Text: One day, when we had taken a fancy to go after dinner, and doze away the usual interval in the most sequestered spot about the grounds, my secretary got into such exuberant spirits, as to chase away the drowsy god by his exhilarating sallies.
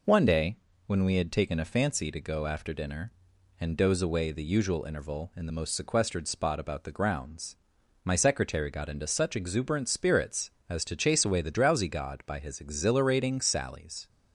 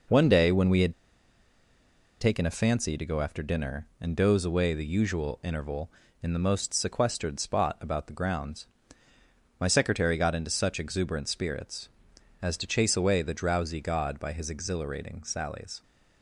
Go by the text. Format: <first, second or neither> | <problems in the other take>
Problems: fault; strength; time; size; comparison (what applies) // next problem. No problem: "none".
first | pauses between "had" and "taken"; strong; at 0.9 s; 1.2 s long